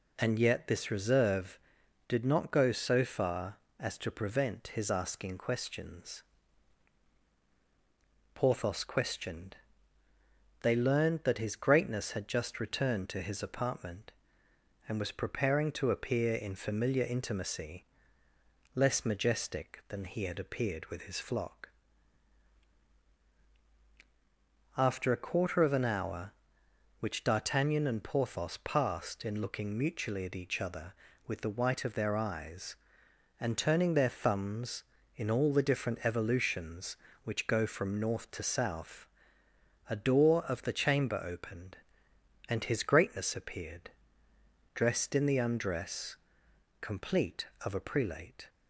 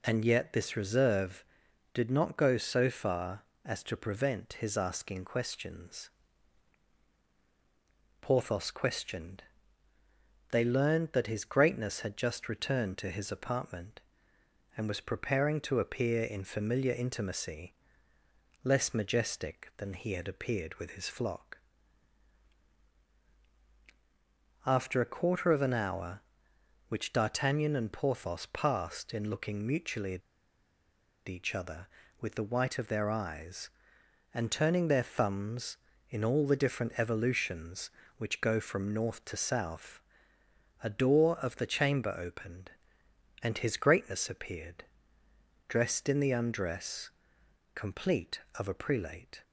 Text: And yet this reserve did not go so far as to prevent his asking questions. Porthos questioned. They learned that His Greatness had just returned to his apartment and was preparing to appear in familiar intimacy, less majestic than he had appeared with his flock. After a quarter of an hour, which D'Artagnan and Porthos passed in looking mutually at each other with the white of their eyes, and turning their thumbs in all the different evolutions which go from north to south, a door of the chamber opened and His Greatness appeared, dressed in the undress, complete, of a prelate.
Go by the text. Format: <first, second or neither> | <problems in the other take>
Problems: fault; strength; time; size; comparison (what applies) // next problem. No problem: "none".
first | pauses between "at" and "each"; at 30.2 s; 1.0 s long